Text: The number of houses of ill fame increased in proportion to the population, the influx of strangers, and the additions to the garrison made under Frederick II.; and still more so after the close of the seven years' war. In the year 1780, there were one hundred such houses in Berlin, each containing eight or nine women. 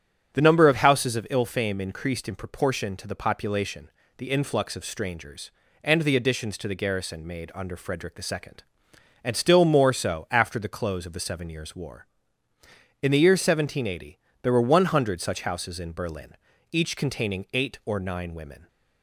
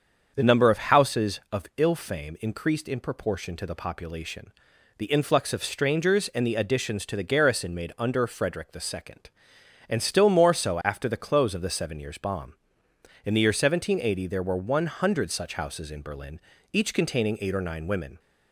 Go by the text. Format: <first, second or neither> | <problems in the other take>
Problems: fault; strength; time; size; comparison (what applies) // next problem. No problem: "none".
first | starts louder than the rest; until 1.3 s; 7 dB; strong in the first // says "bomb" for "war"; at 12.1 s